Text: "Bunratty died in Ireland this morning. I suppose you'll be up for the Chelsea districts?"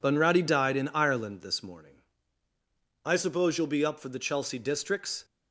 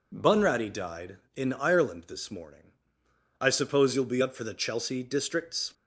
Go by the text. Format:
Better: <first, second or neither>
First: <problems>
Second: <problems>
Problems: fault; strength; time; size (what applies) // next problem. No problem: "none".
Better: second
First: gets quieter; throughout; 7 dB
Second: none